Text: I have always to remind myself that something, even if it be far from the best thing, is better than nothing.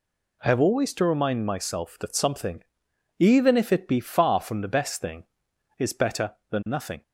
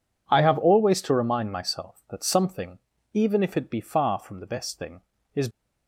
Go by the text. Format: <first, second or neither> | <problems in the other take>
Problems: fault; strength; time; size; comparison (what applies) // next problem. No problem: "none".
first | stops before "better than nothing"; at 5.5 s